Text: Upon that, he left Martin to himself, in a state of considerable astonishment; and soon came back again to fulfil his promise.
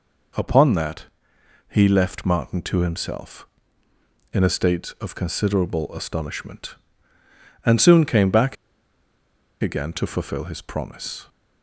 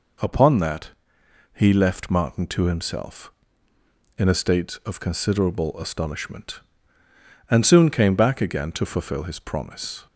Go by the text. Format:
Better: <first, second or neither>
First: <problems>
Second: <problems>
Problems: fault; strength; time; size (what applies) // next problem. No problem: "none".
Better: second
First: pauses between "back" and "again"; at 8.5 s; 1.0 s long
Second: none